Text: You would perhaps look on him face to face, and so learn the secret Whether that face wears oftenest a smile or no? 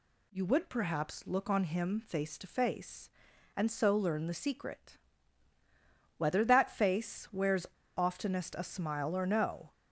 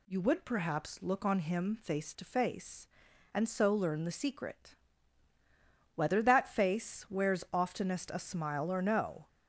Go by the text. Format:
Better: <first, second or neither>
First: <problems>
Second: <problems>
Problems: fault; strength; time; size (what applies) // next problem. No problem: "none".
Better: second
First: pauses between "secret" and "Whether"; at 4.9 s; 1.2 s long // pauses between "wears" and "oftenest"; slight; at 7.6 s; 0.31 s long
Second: pauses between "secret" and "Whether"; at 4.7 s; 1.2 s long